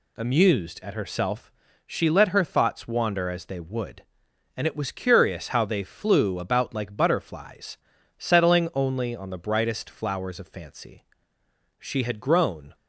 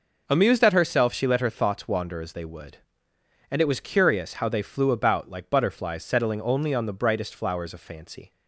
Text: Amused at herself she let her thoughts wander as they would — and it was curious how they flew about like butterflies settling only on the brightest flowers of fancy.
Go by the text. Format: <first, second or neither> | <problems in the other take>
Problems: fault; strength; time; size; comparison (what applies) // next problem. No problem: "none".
second | pauses between "herself" and "she"; slight; at 1.5 s; 0.36 s long // pauses between "butterflies" and "settling"; at 7.7 s; 0.40 s long // goes on to say "She had grown"; noticeable; from 11.7 s on; 0.96 s long